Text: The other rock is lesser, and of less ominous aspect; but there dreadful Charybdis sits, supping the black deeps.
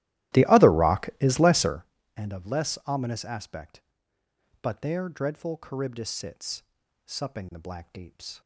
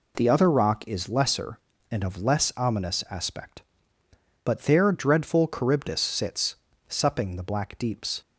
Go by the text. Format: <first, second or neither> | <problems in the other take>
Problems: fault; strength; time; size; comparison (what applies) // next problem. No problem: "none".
second | starts louder than the rest; strong; until 1.9 s; 15 dB